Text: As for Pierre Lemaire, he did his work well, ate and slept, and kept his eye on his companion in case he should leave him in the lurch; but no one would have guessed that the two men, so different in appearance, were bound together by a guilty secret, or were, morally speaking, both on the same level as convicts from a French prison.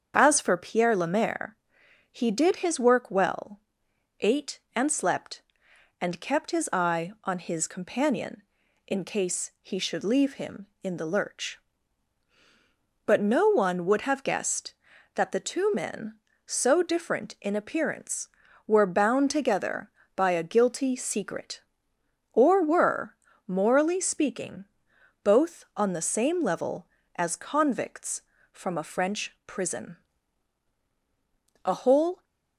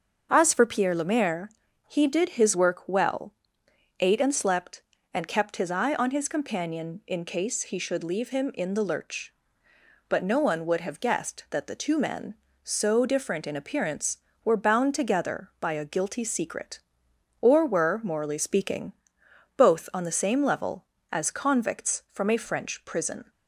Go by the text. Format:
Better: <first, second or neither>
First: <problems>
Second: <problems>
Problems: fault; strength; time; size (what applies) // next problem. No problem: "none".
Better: second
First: starts louder than the rest; strong; until 1.1 s; 7.5 dB // goes on to say "A whole"; from 31.6 s on; 0.58 s long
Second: starts louder than the rest; until 1.3 s; 6.5 dB